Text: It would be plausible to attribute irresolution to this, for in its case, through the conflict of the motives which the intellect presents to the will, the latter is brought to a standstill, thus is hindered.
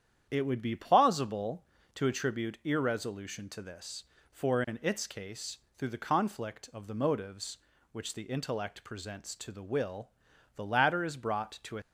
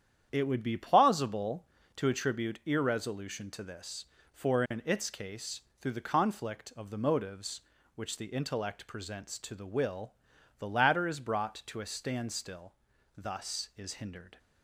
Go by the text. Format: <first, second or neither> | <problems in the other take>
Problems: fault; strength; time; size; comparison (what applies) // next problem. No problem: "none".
second | starts louder than the rest; strong; until 1.3 s; 9.5 dB; strong in the second // stops before "standstill thus is hindered"; at 11.8 s